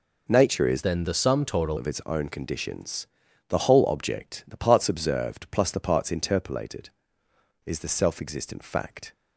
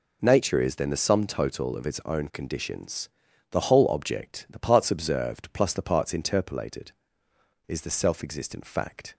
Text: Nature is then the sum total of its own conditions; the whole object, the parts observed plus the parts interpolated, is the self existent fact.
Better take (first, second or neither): second